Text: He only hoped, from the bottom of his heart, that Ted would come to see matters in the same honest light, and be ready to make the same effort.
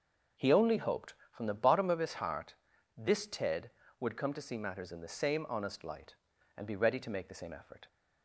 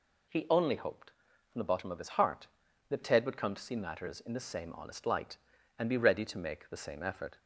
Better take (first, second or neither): second